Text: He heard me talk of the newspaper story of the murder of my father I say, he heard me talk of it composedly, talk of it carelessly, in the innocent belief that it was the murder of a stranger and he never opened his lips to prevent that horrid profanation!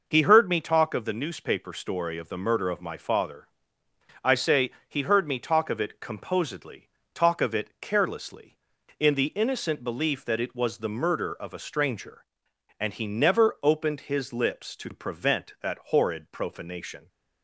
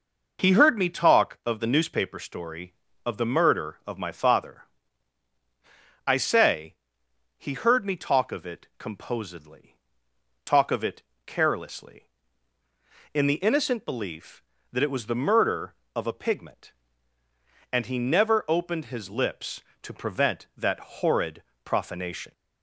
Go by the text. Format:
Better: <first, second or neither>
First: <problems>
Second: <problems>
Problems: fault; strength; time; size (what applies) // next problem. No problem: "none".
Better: first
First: pauses between "father" and "I"; noticeable; at 3.4 s; 0.74 s long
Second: pauses between "father" and "I"; strong; at 4.6 s; 1.4 s long // pauses between "it" and "carelessly"; slight; at 11.0 s; 0.24 s long // says "pigment" for "stranger"; at 16.1 s // pauses between "horrid" and "profanation"; slight; at 21.4 s; 0.22 s long